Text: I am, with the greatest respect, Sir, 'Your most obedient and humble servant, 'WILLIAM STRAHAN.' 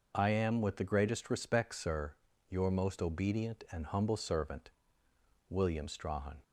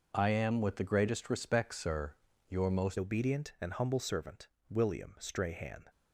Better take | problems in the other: first | changes voice at "obedient"; from 2.9 s on; 2.9 s long

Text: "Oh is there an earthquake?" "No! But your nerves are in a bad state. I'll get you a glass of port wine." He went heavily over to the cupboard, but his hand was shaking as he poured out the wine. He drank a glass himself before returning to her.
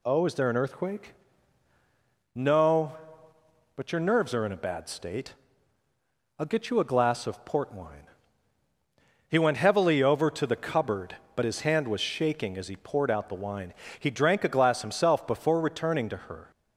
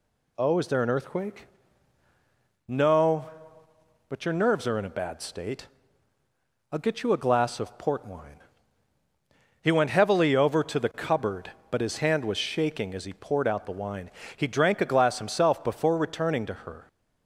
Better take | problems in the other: neither | none

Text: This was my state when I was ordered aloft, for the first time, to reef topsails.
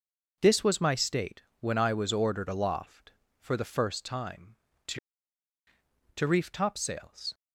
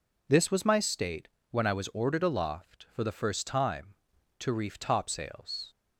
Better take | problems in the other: second | pauses between "state" and "when"; slight; at 1.4 s; 0.18 s long; slight in the second // says "to" twice; at 6.1 s

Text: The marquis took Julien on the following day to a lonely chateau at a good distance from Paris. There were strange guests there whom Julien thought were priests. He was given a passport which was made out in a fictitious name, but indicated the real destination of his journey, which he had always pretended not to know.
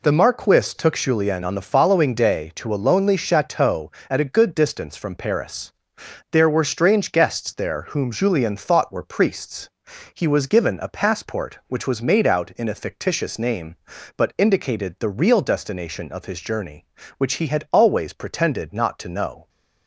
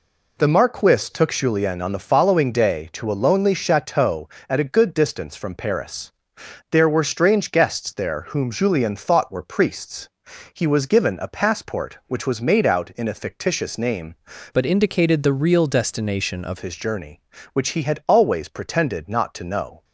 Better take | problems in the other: first | changes voice from "but" to "of"; from 14.5 to 16.5 s; 2.0 s long

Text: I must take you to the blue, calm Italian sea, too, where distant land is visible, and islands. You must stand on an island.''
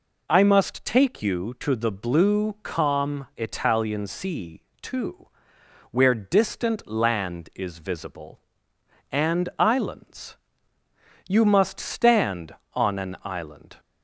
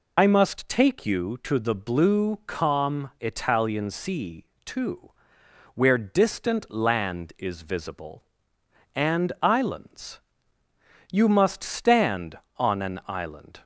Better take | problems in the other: first | loses the start of "I"; at 0.1 s; 55 ms

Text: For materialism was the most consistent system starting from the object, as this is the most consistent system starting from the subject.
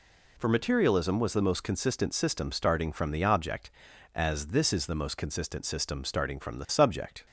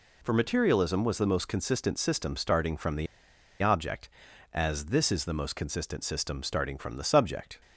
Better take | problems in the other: first | pauses between "the" and "object"; noticeable; at 3.0 s; 0.55 s long

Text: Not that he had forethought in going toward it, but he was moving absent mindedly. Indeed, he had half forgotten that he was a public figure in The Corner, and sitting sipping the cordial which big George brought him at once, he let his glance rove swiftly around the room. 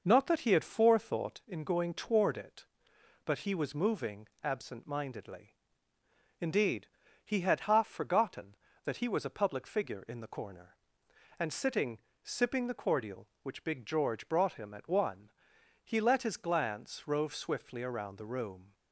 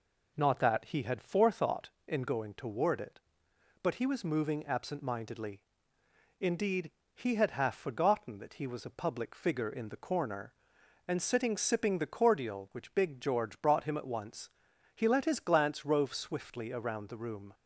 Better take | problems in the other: second | pauses between "moving" and "absent"; slight; at 4.2 s; 0.16 s long // pauses between "sitting" and "sipping"; slight; at 11.9 s; 0.22 s long // says "one" for "once"; at 14.8 s

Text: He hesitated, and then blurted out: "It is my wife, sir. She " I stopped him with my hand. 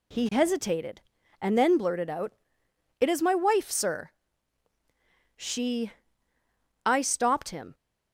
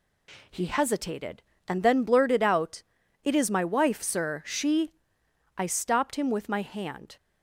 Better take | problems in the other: second | stops before "with my hand"; at 7.7 s

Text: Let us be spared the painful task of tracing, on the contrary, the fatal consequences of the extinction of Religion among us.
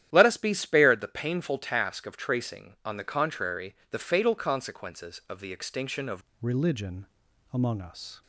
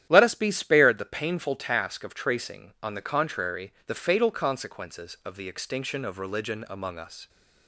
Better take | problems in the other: second | starts louder than the rest; strong; until 1.1 s; 11 dB; strong in the second // changes voice at "Religion"; from 6.4 s on; 1.8 s long // pauses between "Religion" and "among"; noticeable; at 7.0 s; 0.46 s long

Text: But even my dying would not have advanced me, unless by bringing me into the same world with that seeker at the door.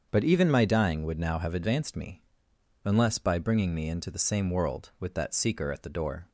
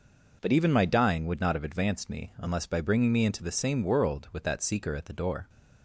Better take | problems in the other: second | starts louder than the rest; until 1.1 s; 7 dB // says "now" for "not"; at 1.1 s

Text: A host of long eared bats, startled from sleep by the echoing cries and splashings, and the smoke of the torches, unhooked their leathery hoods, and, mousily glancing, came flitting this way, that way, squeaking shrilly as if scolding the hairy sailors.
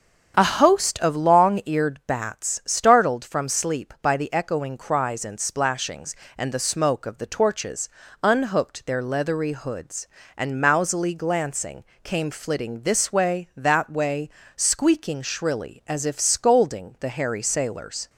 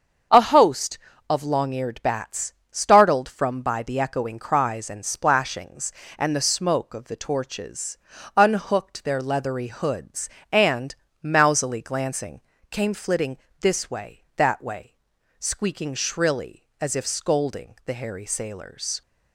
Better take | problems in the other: first | starts louder than the rest; until 1.6 s; 7 dB; strong in the first // skips "sleep"; at 3.6 s // pauses between "flitting" and "this"; slight; at 13.3 s; 0.22 s long

